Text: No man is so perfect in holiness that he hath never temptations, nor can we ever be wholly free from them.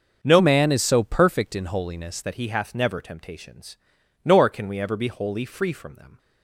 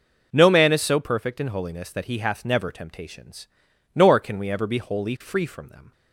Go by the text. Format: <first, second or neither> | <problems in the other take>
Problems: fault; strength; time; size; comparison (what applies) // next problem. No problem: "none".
second | starts louder than the rest; until 1.2 s; 6.5 dB // changes voice from "man" to "holiness"; from 0.3 to 2.2 s; 1.9 s long